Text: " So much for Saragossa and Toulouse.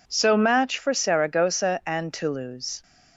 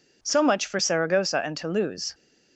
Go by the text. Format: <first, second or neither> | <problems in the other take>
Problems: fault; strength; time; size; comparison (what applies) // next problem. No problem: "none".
second | says "match" for "much"; at 0.3 s